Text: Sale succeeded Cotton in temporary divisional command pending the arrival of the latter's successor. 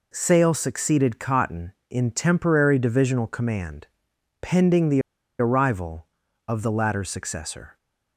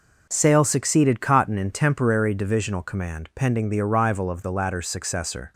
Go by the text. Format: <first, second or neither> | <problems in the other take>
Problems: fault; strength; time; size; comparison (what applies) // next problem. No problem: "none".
second | pauses between "command" and "pending"; noticeable; at 3.8 s; 0.56 s long // pauses between "the" and "arrival"; at 5.0 s; 0.39 s long